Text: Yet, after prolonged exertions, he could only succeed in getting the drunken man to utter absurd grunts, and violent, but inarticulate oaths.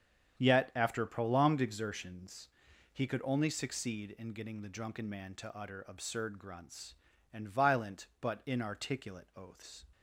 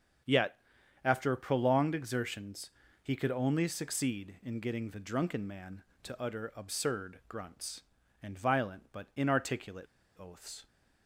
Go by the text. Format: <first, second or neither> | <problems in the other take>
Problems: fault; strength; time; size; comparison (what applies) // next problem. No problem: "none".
first | starts louder than the rest; strong; until 1.7 s; 7.5 dB; strong in the first // pauses between "inarticulate" and "oaths"; slight; at 9.8 s; 0.32 s long